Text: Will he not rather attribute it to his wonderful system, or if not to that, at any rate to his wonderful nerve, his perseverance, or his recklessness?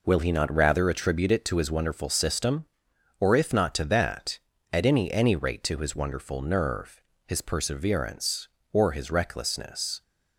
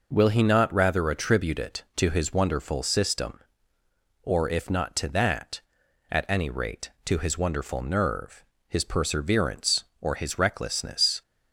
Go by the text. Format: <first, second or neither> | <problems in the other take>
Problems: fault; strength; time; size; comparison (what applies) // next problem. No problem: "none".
second | says "any" twice; at 5.1 s